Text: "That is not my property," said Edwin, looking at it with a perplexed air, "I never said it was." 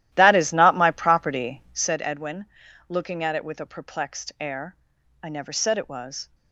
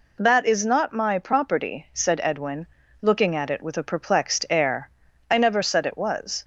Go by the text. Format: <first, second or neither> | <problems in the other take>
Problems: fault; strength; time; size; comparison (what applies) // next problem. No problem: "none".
second | starts louder than the rest; strong; until 2.0 s; 13.5 dB